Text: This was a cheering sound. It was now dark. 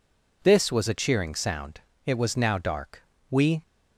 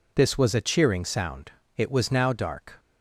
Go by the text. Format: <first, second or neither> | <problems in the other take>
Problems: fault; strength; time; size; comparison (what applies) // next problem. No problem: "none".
second | goes on to say "We"; slight; from 3.2 s on; 0.32 s long